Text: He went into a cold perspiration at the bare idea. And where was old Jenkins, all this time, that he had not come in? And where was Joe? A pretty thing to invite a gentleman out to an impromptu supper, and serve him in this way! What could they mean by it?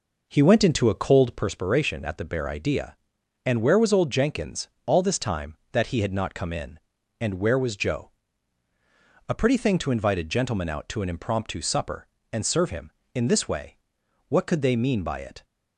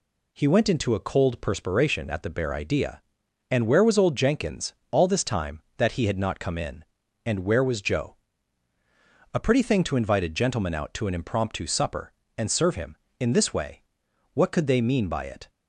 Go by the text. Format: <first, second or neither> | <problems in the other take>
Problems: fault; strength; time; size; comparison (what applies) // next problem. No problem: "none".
second | starts louder than the rest; noticeable; until 1.4 s; 5 dB